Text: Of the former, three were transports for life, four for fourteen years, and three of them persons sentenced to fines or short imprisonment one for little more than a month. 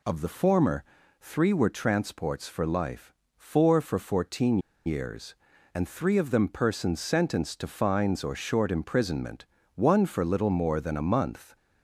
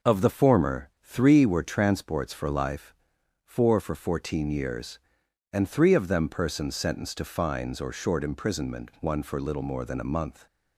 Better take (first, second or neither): second